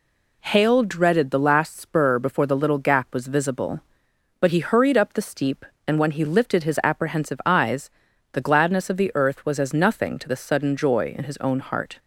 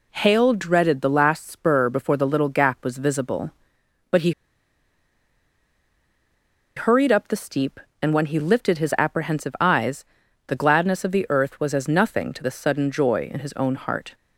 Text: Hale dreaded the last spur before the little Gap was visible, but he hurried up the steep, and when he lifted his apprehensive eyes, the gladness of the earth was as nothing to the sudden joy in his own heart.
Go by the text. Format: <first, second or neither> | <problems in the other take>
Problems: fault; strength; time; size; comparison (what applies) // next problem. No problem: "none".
first | pauses between "he" and "hurried"; strong; at 4.3 s; 2.4 s long